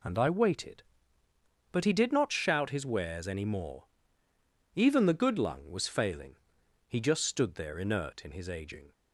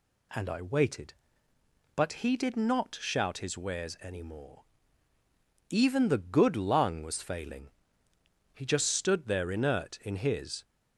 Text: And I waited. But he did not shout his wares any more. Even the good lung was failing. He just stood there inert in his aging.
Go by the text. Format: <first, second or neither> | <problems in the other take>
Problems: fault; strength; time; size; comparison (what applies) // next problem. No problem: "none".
first | stops before "aging"; at 10.6 s